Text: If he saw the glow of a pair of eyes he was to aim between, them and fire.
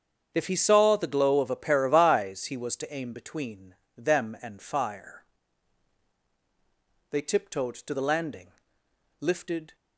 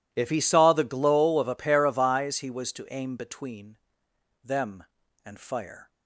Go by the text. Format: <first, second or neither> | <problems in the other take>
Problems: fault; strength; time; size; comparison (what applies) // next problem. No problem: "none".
second | starts louder than the rest; strong; until 1.3 s; 7.5 dB // goes on to say "They tiptoed to the landing lifted"; strong; from 7.1 s on; 2.6 s long